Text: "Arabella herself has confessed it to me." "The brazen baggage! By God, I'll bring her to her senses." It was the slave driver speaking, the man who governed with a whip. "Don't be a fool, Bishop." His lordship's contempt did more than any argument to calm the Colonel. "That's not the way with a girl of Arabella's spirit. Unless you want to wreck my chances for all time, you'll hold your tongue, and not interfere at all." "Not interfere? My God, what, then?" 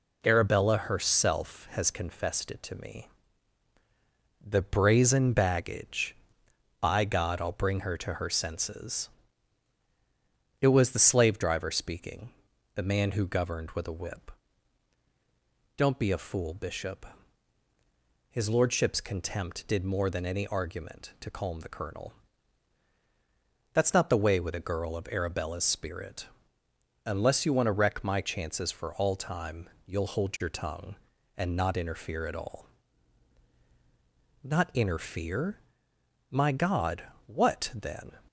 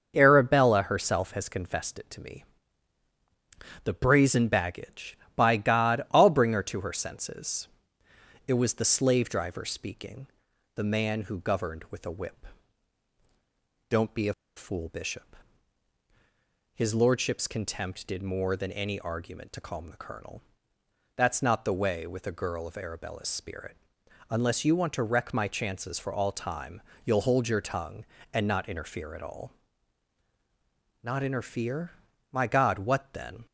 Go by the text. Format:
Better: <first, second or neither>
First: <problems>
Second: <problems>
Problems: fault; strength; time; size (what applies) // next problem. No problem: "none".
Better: first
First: none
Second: starts louder than the rest; until 1.1 s; 6.5 dB // pauses between "a" and "fool"; slight; at 14.3 s; 0.23 s long